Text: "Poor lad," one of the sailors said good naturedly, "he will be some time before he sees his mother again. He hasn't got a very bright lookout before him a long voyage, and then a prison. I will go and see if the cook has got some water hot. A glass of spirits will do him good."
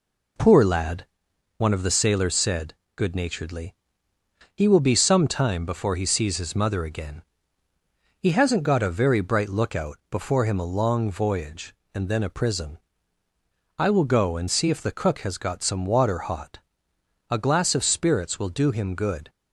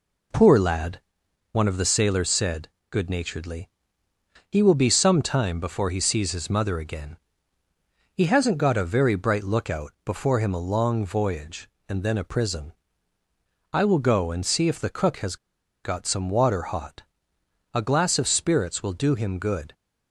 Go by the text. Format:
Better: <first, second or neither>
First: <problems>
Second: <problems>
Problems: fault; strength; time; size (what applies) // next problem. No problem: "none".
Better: first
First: pauses between "said" and "good"; slight; at 2.7 s; 0.20 s long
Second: pauses between "said" and "good"; slight; at 2.6 s; 0.20 s long // pauses between "has" and "got"; noticeable; at 15.3 s; 0.48 s long